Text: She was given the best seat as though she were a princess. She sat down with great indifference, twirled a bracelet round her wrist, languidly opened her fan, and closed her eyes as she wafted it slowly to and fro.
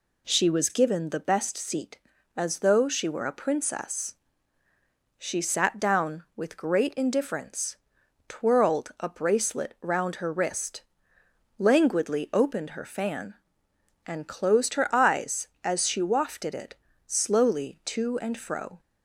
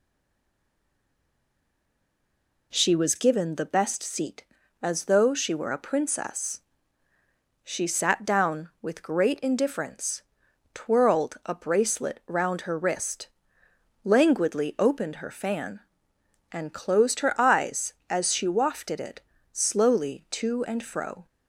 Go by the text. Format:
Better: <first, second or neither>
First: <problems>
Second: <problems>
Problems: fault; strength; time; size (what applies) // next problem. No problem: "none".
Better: first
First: pauses between "it" and "slowly"; slight; at 16.7 s; 0.32 s long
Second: stays silent before the first word; strong; until 2.7 s; 2.7 s long // pauses between "it" and "slowly"; slight; at 19.1 s; 0.32 s long